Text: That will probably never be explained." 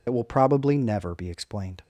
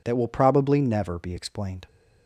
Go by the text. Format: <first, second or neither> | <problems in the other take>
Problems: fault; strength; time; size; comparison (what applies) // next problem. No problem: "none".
second | loses the start of "That"; at 0.0 s; 60 ms